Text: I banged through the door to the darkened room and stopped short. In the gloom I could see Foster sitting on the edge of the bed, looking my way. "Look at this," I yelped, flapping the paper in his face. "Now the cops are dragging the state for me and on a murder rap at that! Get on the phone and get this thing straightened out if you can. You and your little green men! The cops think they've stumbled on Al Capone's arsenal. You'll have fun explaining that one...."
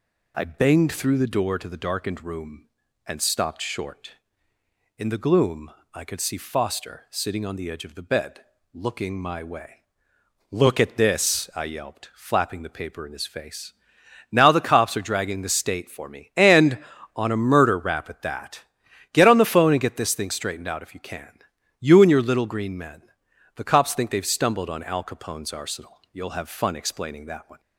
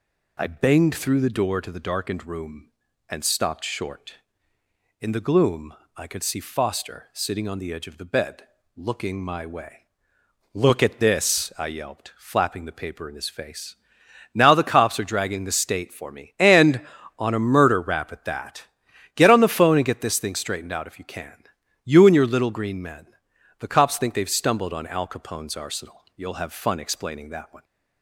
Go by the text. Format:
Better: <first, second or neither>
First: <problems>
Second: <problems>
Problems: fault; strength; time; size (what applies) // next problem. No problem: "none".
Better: neither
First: pauses between "gloom" and "I"; slight; at 5.7 s; 0.22 s long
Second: pauses between "gloom" and "I"; slight; at 5.7 s; 0.22 s long